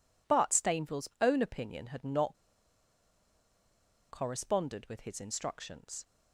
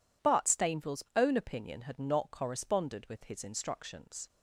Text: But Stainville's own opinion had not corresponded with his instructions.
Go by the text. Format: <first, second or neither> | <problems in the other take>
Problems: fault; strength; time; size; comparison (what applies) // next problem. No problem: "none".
second | pauses between "not" and "corresponded"; strong; at 2.3 s; 1.7 s long